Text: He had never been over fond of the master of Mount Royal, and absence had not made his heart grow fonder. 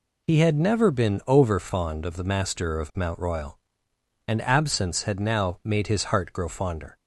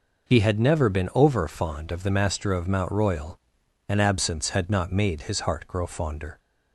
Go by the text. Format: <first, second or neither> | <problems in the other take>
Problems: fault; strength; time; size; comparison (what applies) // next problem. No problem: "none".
second | says "now" for "not"; at 5.2 s